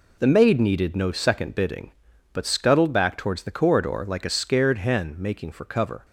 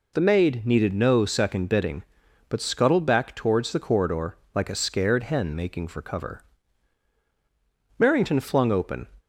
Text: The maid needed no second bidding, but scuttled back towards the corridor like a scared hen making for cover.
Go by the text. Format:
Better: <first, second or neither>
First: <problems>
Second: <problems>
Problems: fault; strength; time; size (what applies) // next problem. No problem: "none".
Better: first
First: none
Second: pauses between "corridor" and "like"; slight; at 4.3 s; 0.18 s long // goes on to say "Merrington flung open"; noticeable; from 8.0 s on; 1.0 s long